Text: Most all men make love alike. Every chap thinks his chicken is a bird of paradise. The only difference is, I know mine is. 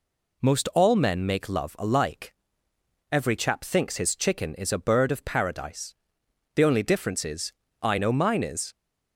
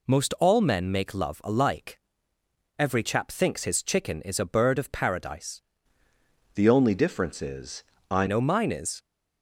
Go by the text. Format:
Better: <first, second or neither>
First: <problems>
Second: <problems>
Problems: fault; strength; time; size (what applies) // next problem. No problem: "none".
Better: first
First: none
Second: changes voice from "The" to "I"; from 6.5 to 8.2 s; 1.7 s long